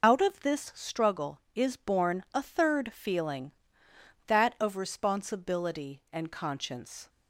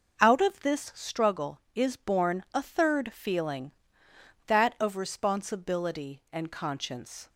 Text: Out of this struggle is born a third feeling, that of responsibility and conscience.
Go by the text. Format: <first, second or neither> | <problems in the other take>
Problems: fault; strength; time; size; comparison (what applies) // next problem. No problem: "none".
second | loses the start of "Out"; at 0.0 s; 45 ms